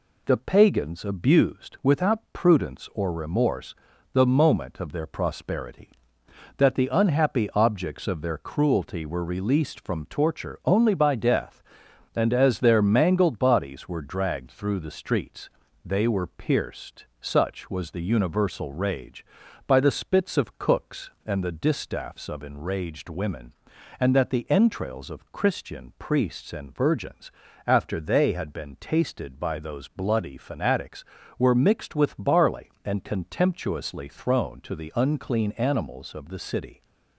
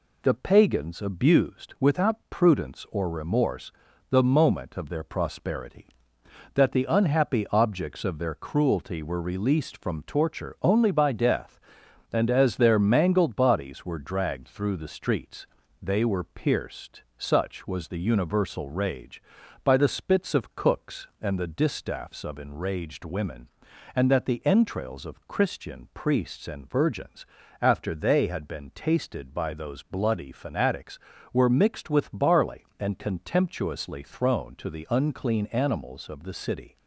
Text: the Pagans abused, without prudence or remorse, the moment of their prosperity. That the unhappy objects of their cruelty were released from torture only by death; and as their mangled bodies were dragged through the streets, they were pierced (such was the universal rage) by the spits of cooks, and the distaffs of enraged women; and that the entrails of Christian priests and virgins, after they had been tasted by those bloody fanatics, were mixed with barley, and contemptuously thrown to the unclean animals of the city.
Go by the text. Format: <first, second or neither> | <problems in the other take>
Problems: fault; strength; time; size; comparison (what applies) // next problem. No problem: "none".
neither | none